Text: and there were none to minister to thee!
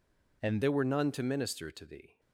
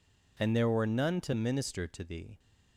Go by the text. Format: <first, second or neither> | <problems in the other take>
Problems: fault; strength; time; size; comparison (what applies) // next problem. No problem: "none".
second | changes voice at "there"; from 0.6 s on; 1.5 s long